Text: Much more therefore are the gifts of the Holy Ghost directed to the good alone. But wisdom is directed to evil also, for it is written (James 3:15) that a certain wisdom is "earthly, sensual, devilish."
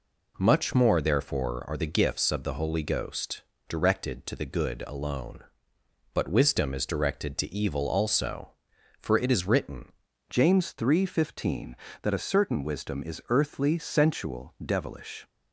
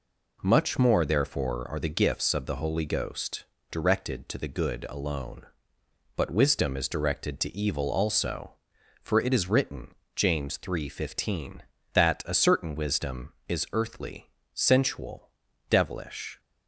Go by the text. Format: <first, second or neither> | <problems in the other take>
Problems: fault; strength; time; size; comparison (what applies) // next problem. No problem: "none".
second | pauses between "Ghost" and "directed"; slight; at 3.4 s; 0.28 s long; slight in the second // changes voice at "James"; from 10.2 s on; 5.0 s long